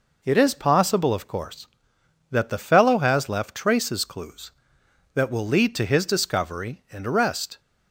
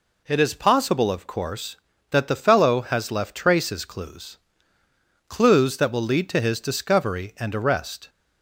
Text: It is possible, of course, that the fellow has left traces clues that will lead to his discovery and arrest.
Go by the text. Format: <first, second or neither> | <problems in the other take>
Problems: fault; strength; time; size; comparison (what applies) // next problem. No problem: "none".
first | says "clues" twice; at 5.2 s